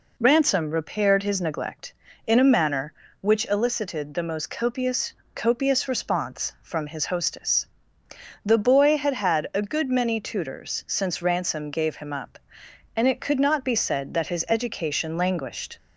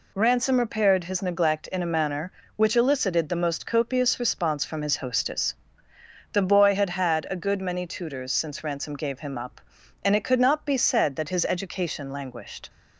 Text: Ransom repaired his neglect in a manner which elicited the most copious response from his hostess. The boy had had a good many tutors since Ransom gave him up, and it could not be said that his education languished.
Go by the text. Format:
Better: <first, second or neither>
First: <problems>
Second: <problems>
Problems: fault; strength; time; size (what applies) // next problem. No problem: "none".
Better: second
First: says "copious" twice; at 5.3 s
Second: none